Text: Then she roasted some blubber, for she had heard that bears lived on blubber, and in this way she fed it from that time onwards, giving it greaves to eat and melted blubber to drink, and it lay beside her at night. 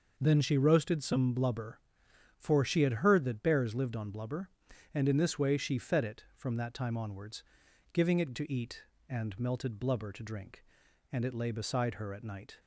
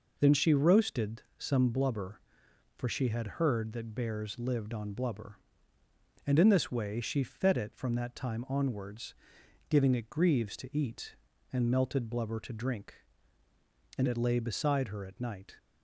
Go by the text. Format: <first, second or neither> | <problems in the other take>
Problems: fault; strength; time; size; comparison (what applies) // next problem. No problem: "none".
second | skips "greaves"; at 8.3 s